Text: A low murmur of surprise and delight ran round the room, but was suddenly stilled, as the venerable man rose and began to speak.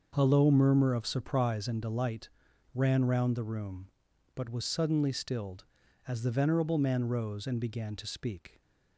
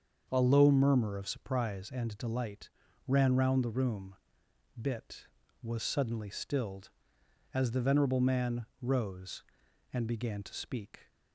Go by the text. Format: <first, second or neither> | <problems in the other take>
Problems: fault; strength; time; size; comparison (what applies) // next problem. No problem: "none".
first | starts louder than the rest; until 1.3 s; 7 dB; also in the first // pauses between "delight" and "ran"; at 2.6 s; 0.38 s long; also in the first // says "bit" for "but"; at 4.7 s // pauses between "man" and "rose"; slight; at 8.6 s; 0.16 s long